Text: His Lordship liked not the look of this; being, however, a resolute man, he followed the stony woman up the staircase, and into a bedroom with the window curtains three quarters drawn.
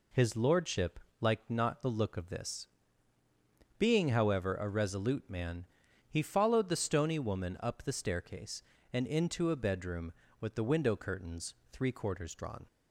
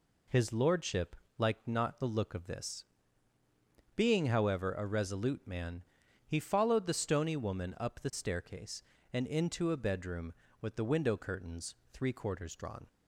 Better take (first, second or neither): neither